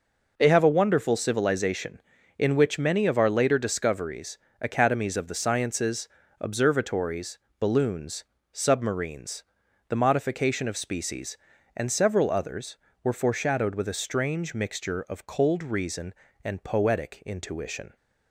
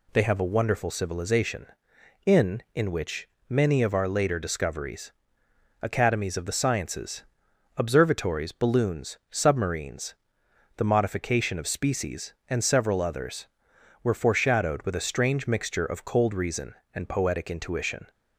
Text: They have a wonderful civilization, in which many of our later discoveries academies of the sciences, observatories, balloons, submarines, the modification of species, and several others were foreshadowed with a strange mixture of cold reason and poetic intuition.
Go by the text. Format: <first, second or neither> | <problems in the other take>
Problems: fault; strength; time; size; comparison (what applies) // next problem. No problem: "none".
first | says "in" twice; at 2.7 s // pauses between "which" and "many"; slight; at 3.2 s; 0.20 s long // pauses between "discoveries" and "academies"; noticeable; at 5.1 s; 0.70 s long; slight in the first